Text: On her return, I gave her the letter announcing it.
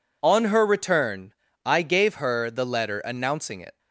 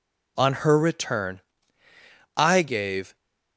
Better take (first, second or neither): first